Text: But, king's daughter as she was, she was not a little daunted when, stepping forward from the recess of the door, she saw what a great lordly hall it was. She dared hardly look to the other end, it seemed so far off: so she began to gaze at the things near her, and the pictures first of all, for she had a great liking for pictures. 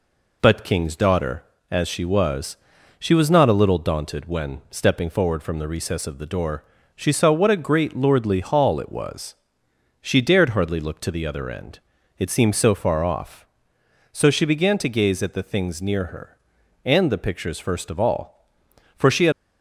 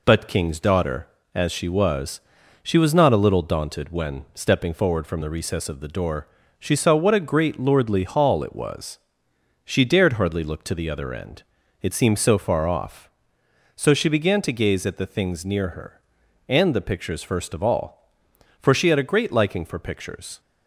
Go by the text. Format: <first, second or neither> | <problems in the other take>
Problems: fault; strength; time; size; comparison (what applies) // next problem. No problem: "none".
second | stops before "a great liking for pictures"; at 19.3 s